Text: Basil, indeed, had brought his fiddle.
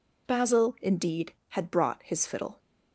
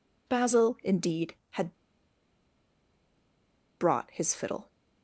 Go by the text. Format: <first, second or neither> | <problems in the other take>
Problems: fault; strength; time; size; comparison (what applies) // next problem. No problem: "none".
first | pauses between "had" and "brought"; strong; at 1.7 s; 2.0 s long